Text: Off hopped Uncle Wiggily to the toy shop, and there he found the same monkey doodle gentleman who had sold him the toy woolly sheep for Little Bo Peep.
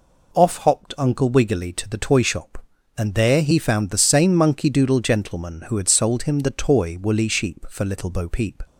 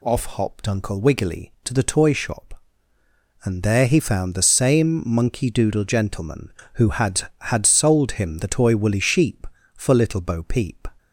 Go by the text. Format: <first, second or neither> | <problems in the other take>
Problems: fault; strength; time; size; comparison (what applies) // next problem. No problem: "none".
first | says "had" twice; at 7.4 s